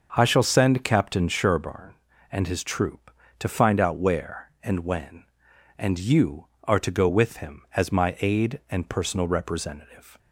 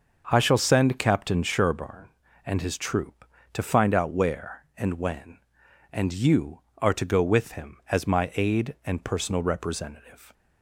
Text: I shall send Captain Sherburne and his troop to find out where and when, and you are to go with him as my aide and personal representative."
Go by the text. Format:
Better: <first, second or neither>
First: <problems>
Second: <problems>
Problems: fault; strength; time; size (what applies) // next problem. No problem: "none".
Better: neither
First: starts louder than the rest; until 1.1 s; 6.5 dB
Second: starts louder than the rest; until 1.3 s; 6.5 dB